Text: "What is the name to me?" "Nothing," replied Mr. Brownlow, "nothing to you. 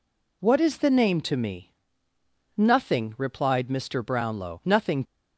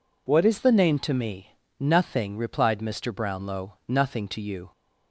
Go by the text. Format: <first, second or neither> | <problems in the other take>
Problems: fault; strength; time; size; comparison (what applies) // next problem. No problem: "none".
second | stops before "to you"; at 5.0 s